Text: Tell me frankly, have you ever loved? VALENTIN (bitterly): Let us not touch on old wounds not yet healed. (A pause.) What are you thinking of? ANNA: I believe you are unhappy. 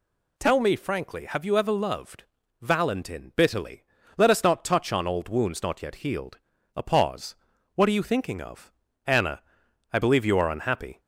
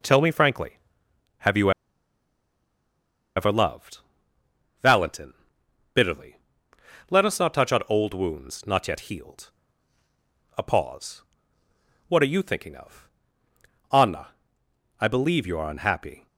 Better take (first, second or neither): first